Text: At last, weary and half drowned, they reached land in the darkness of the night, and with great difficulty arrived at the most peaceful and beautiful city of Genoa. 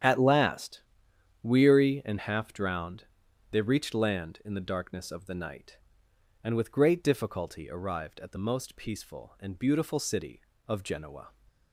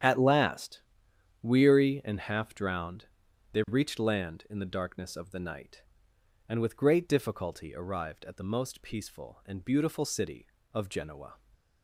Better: neither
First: starts louder than the rest; strong; until 1.6 s; 9 dB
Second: starts louder than the rest; strong; until 1.6 s; 9 dB

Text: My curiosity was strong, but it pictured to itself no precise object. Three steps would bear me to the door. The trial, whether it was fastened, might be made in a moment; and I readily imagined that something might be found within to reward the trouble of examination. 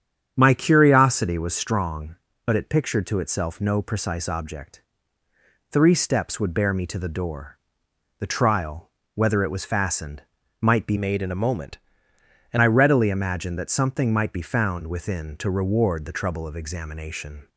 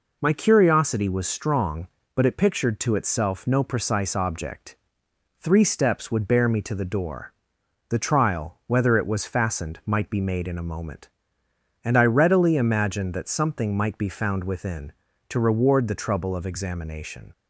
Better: second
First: starts louder than the rest; strong; until 1.3 s; 8 dB // changes voice from "made" to "and"; from 10.9 to 12.5 s; 1.6 s long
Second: none

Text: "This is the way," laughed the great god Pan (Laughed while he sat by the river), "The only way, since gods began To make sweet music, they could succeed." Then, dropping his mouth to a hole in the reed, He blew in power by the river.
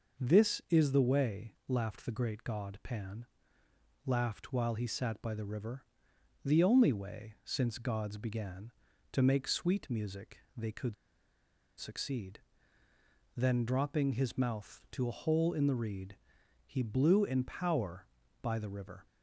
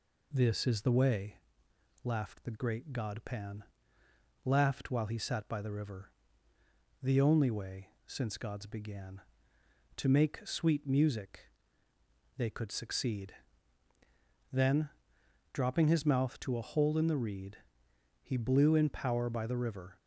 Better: second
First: pauses between "could" and "succeed"; noticeable; at 10.9 s; 0.83 s long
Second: none

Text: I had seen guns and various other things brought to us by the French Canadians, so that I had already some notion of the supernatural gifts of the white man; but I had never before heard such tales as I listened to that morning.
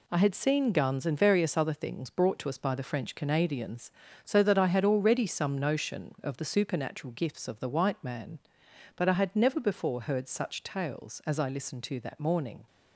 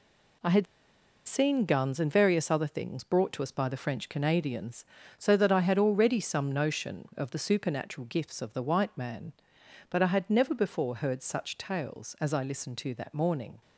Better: first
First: none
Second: pauses between "had" and "seen"; noticeable; at 0.6 s; 0.63 s long

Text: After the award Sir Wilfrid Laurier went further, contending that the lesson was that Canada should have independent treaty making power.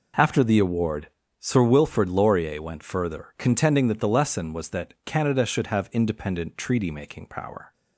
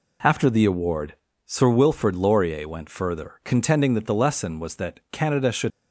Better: first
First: pauses between "award" and "Sir"; slight; at 1.0 s; 0.32 s long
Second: pauses between "award" and "Sir"; slight; at 1.1 s; 0.32 s long // stops before "have independent treaty making power"; at 5.7 s

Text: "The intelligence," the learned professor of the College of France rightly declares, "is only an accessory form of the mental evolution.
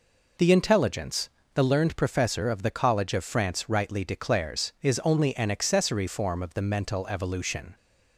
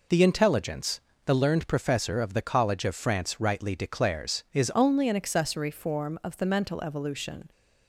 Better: first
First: none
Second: changes voice at "only"; from 4.7 s on; 2.8 s long

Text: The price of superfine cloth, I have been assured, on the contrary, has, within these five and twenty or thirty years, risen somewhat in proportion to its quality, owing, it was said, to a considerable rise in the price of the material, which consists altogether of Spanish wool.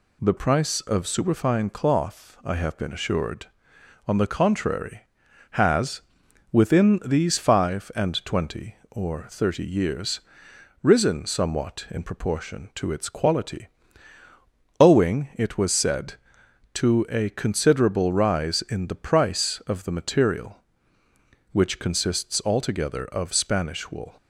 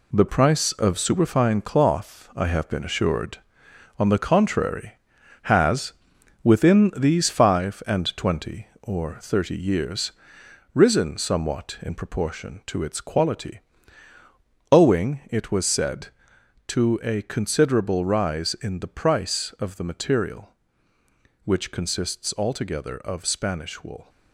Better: first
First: none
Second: gets quieter; throughout; 7 dB

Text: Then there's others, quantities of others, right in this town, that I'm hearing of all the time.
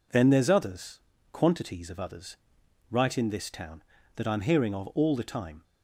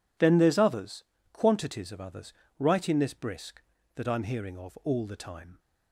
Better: first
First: none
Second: says "brisk" for "town"; at 3.1 s

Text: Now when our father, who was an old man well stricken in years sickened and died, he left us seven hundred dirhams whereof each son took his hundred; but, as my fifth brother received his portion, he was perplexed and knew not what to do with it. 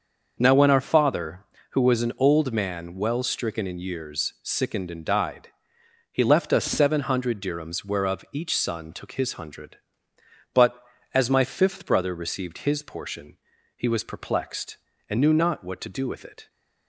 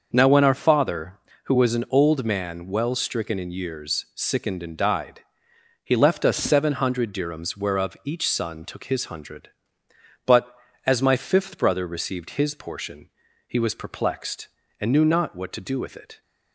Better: neither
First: starts louder than the rest; until 1.3 s; 6 dB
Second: starts louder than the rest; until 1.1 s; 6 dB

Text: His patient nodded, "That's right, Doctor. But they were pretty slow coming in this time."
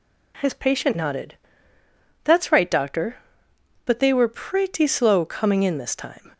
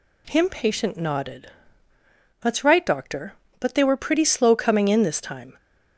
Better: first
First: none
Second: says "Him" for "His"; at 0.2 s

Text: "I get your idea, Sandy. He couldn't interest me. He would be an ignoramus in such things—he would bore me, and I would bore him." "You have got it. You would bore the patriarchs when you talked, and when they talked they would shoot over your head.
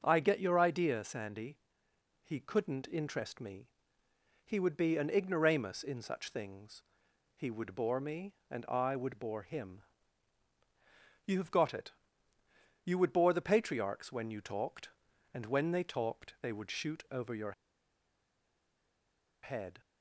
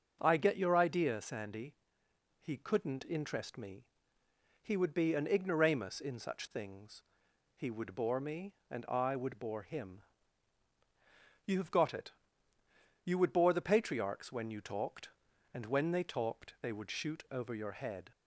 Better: second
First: starts louder than the rest; until 1.0 s; 6.5 dB // pauses between "your" and "head"; strong; at 17.5 s; 1.9 s long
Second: starts louder than the rest; until 1.2 s; 6 dB

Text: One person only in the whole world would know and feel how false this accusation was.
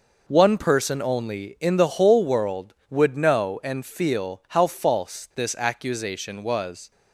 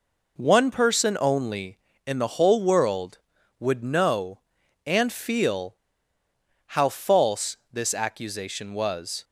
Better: first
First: none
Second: pauses between "feel" and "how"; noticeable; at 5.7 s; 0.92 s long // pauses between "false" and "this"; slight; at 7.5 s; 0.16 s long

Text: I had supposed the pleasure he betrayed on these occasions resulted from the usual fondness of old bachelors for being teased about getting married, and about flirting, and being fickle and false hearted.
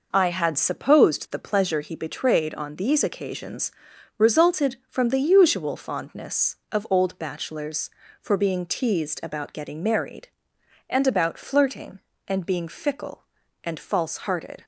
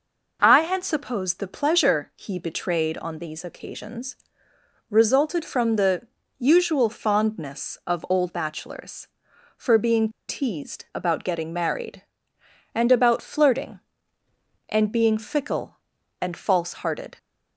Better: first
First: pauses between "occasions" and "resulted"; at 3.7 s; 0.44 s long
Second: pauses between "occasions" and "resulted"; noticeable; at 4.1 s; 0.72 s long // pauses between "the" and "usual"; slight; at 6.0 s; 0.36 s long // pauses between "being" and "teased"; slight; at 10.0 s; 0.20 s long

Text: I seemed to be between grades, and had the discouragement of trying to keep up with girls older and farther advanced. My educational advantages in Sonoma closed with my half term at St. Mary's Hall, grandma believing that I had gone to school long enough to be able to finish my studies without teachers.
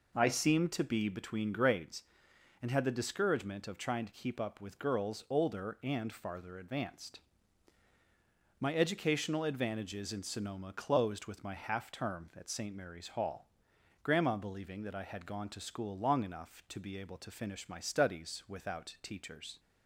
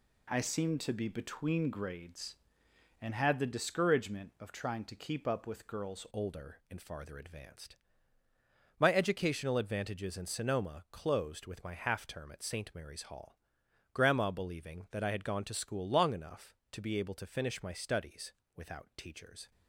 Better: first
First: none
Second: changes voice at "older"; from 6.1 s on; 13.4 s long // pauses between "studies" and "without"; slight; at 18.3 s; 0.22 s long

